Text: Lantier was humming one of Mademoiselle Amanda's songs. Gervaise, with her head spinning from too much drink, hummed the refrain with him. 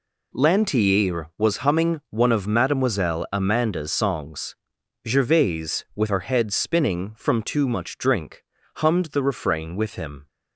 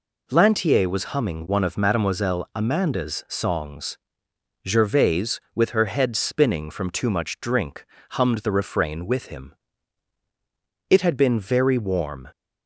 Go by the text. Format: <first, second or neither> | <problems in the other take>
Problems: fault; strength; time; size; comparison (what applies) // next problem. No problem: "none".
first | goes on to say "It had been very warm"; from 10.8 s on; 1.3 s long